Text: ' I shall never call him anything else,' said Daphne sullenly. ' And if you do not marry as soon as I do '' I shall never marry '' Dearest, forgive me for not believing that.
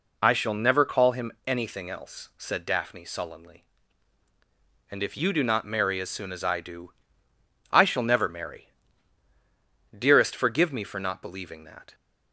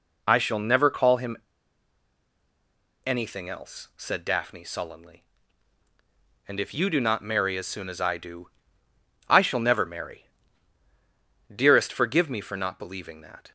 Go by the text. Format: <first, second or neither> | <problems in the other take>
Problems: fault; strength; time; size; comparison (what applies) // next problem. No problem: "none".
first | pauses between "him" and "anything"; strong; at 1.3 s; 1.6 s long